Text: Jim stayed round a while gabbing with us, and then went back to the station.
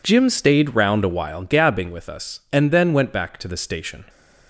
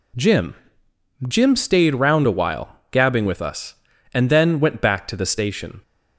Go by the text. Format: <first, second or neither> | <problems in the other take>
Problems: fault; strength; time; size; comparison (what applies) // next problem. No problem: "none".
first | says "Jim" twice; at 1.2 s